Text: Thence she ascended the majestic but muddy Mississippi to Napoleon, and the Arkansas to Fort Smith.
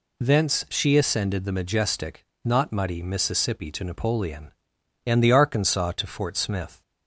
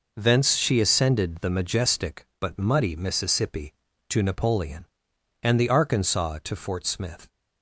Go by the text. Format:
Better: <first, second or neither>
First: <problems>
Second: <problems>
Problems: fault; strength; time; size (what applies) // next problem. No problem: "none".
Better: second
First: says "not" for "but"; at 2.4 s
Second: none